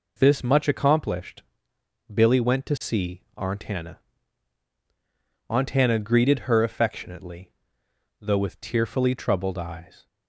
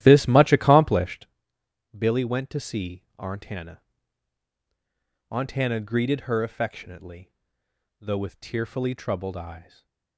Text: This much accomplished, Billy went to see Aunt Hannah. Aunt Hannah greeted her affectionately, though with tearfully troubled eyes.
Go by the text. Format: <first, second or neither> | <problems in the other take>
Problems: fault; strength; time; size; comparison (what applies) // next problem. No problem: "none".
first | starts louder than the rest; strong; until 1.2 s; 13.5 dB // stays silent after the last word; slight; from 9.6 s on; 0.5 s long